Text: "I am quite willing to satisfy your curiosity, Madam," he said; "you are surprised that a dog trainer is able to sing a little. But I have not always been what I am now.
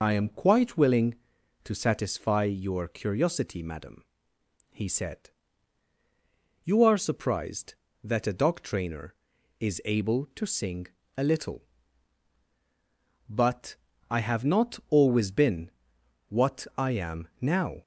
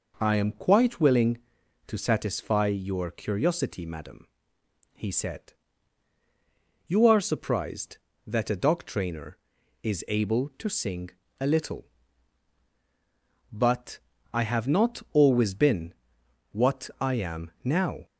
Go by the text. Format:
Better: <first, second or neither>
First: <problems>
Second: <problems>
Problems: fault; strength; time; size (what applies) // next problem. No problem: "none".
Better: second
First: loses the start of "I"; at 0.0 s; 80 ms // pauses between "sing" and "a"; slight; at 10.8 s; 0.30 s long // pauses between "But" and "I"; slight; at 13.7 s; 0.34 s long // pauses between "been" and "what"; noticeable; at 15.6 s; 0.60 s long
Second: pauses between "sing" and "a"; slight; at 11.1 s; 0.30 s long // pauses between "But" and "I"; slight; at 13.9 s; 0.34 s long // pauses between "been" and "what"; noticeable; at 15.9 s; 0.60 s long